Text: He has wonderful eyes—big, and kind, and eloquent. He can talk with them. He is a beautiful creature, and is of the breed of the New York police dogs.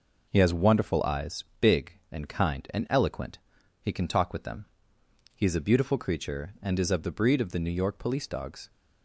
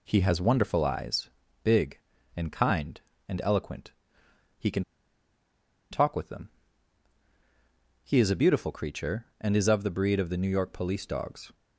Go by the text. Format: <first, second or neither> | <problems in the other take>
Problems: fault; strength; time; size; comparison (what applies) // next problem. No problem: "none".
first | pauses between "can" and "talk"; at 4.8 s; 1.0 s long